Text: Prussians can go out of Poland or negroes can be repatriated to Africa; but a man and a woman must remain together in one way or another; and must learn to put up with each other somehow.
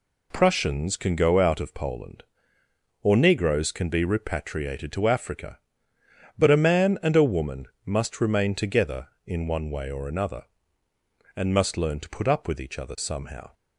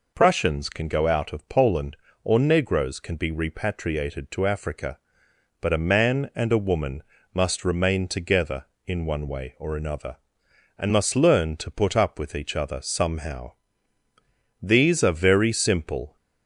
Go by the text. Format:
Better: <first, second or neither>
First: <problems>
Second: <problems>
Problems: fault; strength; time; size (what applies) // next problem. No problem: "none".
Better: first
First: pauses between "woman" and "must"; slight; at 7.6 s; 0.18 s long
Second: pauses between "woman" and "must"; slight; at 7.0 s; 0.30 s long // goes on to say "These are very simple"; from 14.6 s on; 1.5 s long